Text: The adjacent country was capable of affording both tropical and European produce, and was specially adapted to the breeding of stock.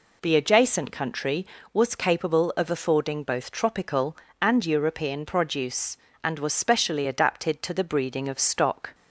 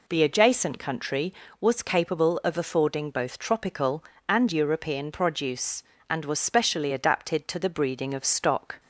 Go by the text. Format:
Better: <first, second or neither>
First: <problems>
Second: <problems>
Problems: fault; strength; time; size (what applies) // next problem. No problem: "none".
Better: neither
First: none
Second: none